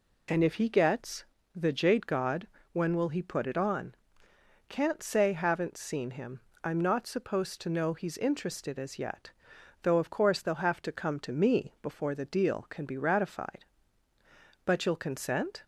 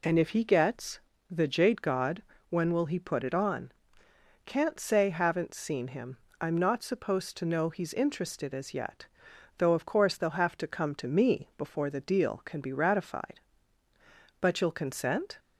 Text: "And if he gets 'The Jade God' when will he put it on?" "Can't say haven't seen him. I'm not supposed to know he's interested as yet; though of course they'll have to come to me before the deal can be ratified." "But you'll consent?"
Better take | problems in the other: neither | pauses between "gets" and "The"; slight; the same in both // pauses between "God" and "when"; slight; the same in both

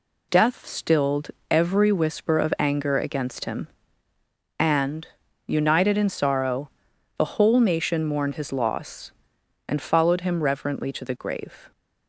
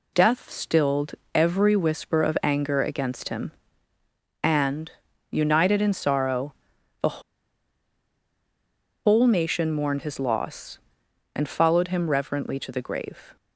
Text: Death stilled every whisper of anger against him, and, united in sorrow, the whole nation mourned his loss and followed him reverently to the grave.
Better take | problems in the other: first | pauses between "stilled" and "every"; slight; at 1.1 s; 0.20 s long; slight in the first // pauses between "the" and "whole"; strong; at 7.2 s; 1.8 s long

